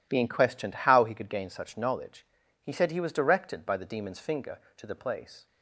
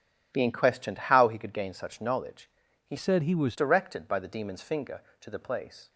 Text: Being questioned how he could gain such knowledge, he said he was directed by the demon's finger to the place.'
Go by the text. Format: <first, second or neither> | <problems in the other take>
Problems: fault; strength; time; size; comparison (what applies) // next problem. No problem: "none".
first | changes voice from "said" to "was"; from 2.9 to 3.5 s; 0.6 s long